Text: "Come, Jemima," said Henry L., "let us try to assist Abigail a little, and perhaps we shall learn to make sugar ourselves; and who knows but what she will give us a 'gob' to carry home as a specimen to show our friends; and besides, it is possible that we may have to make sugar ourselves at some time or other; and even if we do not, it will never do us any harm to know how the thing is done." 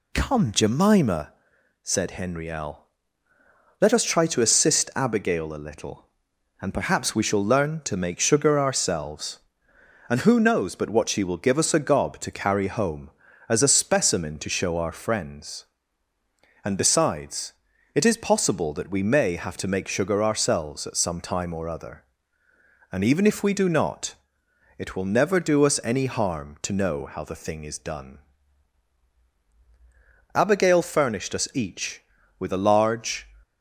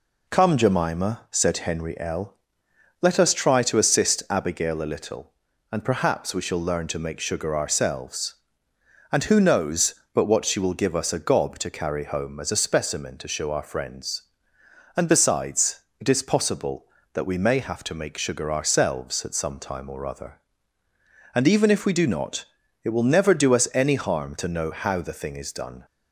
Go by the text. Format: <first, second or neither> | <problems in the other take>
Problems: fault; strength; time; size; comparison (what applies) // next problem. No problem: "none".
second | goes on to say "Abigail furnished us each with a large"; strong; from 30.3 s on; 2.9 s long